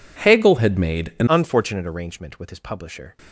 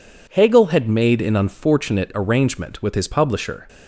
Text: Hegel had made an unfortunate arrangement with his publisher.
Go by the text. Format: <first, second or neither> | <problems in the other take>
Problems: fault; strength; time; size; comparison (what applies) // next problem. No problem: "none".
second | changes voice at "unfortunate"; from 1.2 s on; 1.9 s long